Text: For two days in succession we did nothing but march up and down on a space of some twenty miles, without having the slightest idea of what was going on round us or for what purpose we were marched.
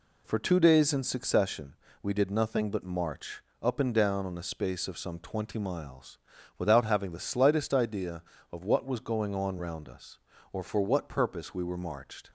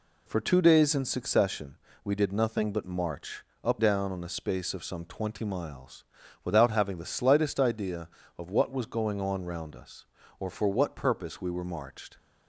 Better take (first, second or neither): first